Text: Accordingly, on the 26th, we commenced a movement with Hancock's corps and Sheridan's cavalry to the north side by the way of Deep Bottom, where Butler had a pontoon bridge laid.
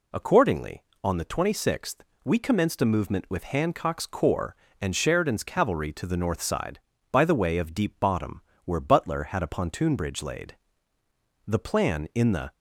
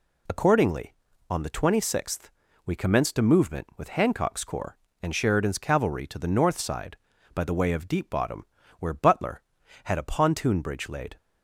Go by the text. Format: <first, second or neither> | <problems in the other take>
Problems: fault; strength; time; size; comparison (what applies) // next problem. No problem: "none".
second | goes on to say "The plan in the"; noticeable; from 11.4 s on; 1.0 s long